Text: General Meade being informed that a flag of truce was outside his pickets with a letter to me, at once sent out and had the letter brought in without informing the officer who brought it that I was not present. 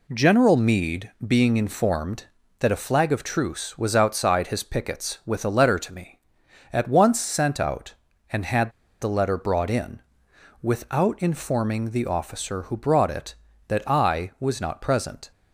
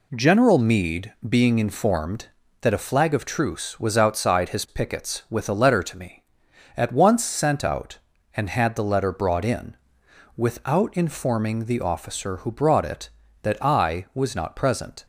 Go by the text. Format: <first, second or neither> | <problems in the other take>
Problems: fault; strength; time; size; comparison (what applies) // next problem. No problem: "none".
second | pauses between "Meade" and "being"; slight; at 1.0 s; 0.16 s long; slight in the second // pauses between "had" and "the"; slight; at 8.6 s; 0.32 s long // pauses between "in" and "without"; noticeable; at 10.0 s; 0.60 s long; noticeable in the second